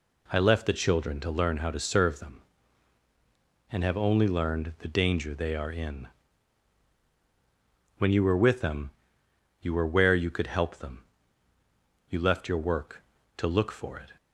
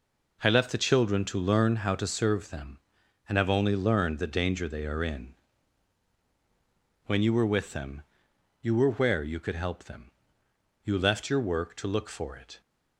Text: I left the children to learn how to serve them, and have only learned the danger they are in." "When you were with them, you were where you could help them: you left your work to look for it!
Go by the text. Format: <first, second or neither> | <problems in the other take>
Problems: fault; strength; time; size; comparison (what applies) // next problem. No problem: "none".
neither | none